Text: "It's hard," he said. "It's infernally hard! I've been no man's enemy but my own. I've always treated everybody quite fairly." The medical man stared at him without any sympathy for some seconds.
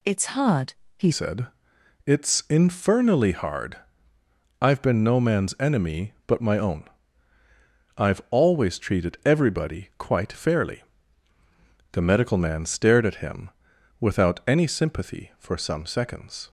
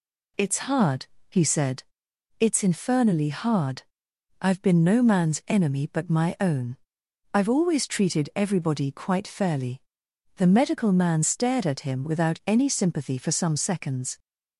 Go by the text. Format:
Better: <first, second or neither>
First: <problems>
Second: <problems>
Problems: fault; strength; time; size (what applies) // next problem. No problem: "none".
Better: second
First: changes voice at "said"; from 1.1 s on; 15.3 s long // pauses between "him" and "without"; noticeable; at 13.4 s; 0.50 s long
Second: none